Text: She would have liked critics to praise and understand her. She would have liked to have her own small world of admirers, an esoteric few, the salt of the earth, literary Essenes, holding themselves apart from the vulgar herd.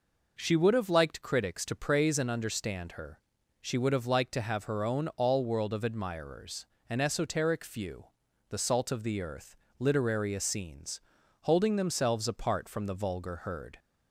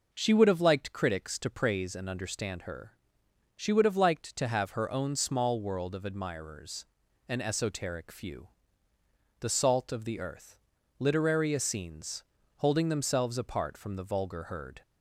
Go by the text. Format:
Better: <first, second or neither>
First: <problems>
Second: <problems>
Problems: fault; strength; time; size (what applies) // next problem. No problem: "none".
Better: second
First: says "all" for "small"; at 5.1 s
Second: none